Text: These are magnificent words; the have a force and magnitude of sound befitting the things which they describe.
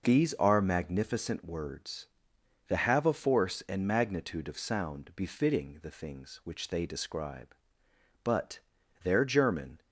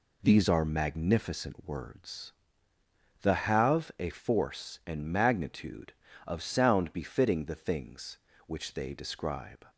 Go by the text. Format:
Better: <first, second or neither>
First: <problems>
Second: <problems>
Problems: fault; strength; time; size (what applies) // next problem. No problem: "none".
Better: second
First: goes on to say "But their German"; from 8.2 s on; 1.5 s long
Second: none